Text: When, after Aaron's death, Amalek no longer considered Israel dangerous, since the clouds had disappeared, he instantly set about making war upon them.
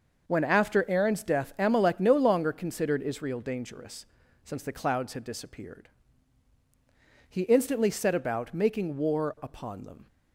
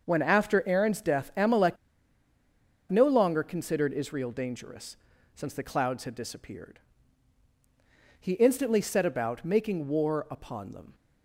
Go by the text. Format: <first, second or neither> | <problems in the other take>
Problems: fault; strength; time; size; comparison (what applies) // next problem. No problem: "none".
first | pauses between "Amalek" and "no"; at 1.7 s; 1.1 s long